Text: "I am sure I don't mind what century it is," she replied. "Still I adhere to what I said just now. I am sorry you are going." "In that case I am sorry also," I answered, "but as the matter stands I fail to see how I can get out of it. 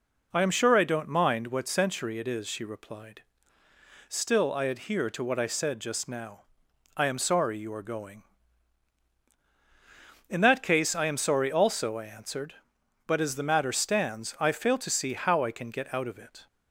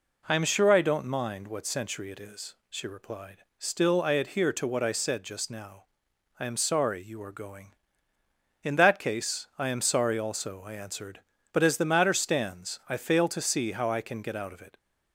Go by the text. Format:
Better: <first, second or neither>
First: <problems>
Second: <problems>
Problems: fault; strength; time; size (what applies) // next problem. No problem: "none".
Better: neither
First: none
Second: none